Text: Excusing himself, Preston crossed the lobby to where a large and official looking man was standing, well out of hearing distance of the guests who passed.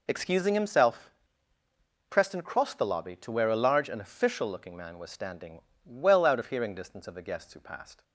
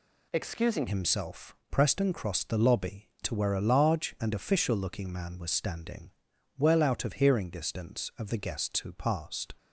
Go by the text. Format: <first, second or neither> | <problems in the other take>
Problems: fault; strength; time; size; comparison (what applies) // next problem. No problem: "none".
first | changes voice at "himself"; from 0.8 s on; 8.7 s long